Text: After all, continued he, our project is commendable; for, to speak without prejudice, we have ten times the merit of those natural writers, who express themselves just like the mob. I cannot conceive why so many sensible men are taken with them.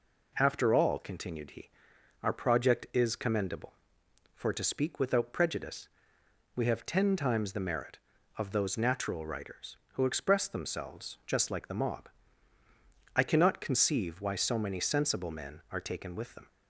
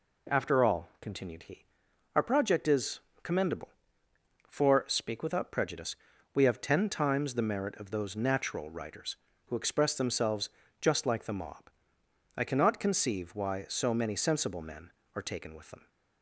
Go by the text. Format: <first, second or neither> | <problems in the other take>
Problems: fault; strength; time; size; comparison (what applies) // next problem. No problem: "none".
first | pauses between "is" and "commendable"; slight; at 2.9 s; 0.24 s long // skips "to"; at 4.8 s // pauses between "themselves" and "just"; slight; at 10.4 s; 0.32 s long